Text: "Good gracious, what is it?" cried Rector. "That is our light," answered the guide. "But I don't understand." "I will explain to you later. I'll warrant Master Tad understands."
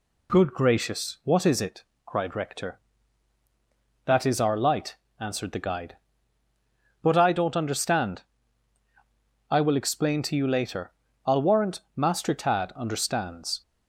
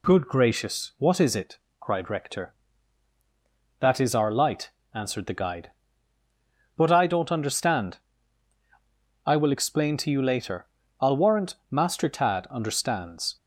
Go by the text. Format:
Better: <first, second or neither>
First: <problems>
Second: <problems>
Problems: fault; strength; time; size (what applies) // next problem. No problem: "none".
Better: neither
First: pauses between "warrant" and "Master"; slight; at 11.7 s; 0.16 s long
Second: pauses between "warrant" and "Master"; slight; at 11.5 s; 0.16 s long